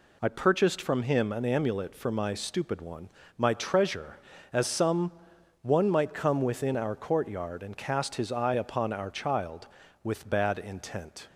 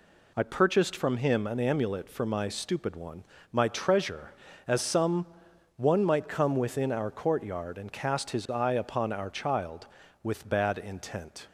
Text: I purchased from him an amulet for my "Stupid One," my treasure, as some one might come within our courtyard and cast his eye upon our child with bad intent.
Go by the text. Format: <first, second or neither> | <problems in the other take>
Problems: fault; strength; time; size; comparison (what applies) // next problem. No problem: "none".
neither | pauses between "some" and "one"; noticeable; the same in both